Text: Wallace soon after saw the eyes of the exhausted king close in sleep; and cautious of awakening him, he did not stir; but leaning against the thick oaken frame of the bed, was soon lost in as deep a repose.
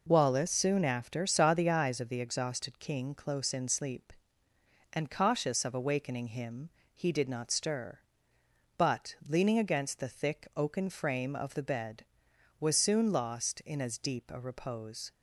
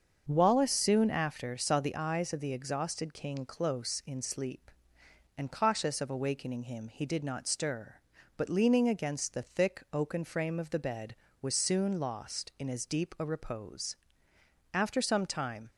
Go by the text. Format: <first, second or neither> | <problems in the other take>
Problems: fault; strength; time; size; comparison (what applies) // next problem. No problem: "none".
first | starts louder than the rest; until 1.2 s; 7 dB // goes on to say "After some time"; noticeable; from 14.7 s on; 0.96 s long